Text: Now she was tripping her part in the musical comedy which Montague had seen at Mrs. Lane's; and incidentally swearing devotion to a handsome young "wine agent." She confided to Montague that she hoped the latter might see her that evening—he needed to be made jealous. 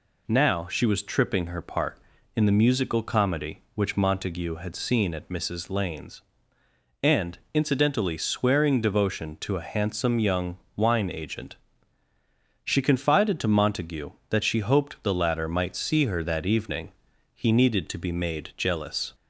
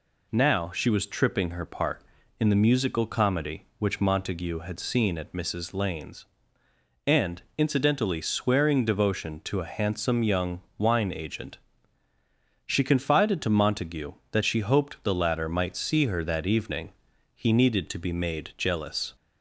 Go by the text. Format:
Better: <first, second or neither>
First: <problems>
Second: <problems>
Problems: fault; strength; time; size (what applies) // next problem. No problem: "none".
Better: neither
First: pauses between "young" and "wine"; slight; at 10.5 s; 0.18 s long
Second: pauses between "young" and "wine"; slight; at 10.6 s; 0.16 s long